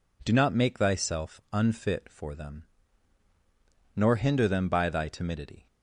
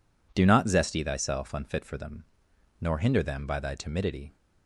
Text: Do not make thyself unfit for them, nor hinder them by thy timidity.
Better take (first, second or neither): first